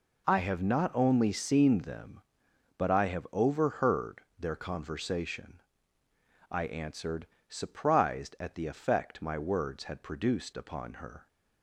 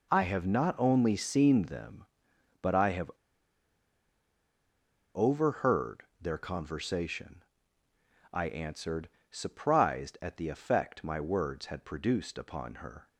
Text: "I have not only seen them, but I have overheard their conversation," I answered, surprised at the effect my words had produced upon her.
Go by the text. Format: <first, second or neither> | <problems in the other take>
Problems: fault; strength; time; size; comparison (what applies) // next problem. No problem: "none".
first | pauses between "have" and "overheard"; strong; at 3.1 s; 2.0 s long // pauses between "overheard" and "their"; slight; at 6.0 s; 0.16 s long; slight in the first